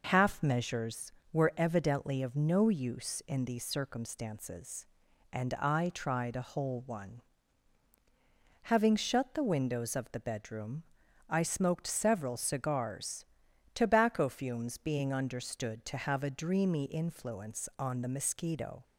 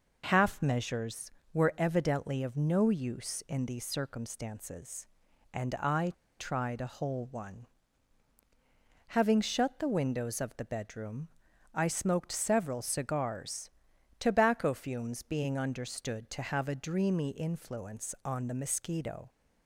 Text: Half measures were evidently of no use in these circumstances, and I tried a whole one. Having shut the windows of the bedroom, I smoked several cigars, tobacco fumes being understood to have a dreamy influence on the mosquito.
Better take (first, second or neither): first